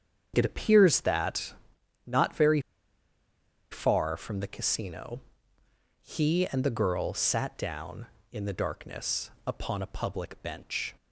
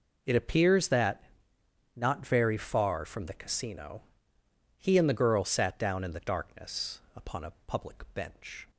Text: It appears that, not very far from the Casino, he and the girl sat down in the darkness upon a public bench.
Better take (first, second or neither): second